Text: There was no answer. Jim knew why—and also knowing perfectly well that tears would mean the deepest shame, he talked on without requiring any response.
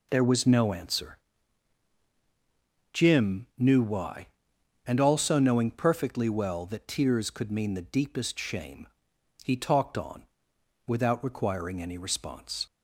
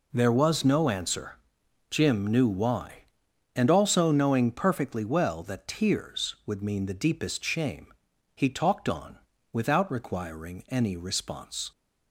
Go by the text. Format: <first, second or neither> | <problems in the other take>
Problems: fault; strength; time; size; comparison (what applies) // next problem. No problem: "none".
second | says "could" for "would"; at 7.2 s // pauses between "on" and "without"; noticeable; at 10.2 s; 0.62 s long; slight in the second